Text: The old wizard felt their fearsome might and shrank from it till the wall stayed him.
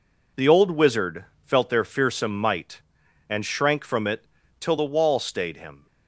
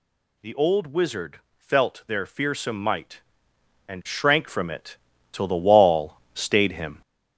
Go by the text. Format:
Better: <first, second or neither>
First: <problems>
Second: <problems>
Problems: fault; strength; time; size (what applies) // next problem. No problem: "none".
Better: first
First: pauses between "wizard" and "felt"; slight; at 1.2 s; 0.18 s long // pauses between "it" and "till"; slight; at 4.2 s; 0.36 s long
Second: gets louder; throughout; 6.5 dB // pauses between "wizard" and "felt"; slight; at 1.3 s; 0.16 s long // pauses between "it" and "till"; slight; at 4.9 s; 0.34 s long // pauses between "wall" and "stayed"; slight; at 6.1 s; 0.18 s long